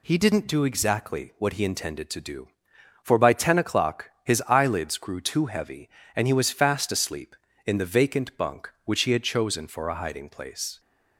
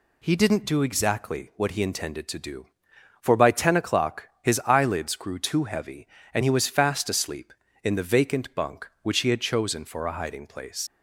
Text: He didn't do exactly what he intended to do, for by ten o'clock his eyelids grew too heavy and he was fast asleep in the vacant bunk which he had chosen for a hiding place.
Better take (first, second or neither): first